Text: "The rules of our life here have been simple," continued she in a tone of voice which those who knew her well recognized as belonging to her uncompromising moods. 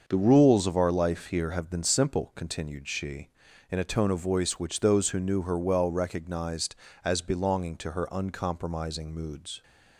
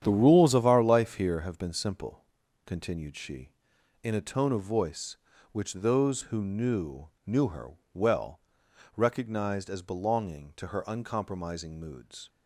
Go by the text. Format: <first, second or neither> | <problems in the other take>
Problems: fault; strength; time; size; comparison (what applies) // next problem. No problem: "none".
first | starts louder than the rest; strong; until 1.0 s; 9 dB; also in the first // says "knew" twice; at 7.2 s // pauses between "her" and "well"; slight; at 7.7 s; 0.16 s long // pauses between "well" and "recognized"; noticeable; at 8.4 s; 0.56 s long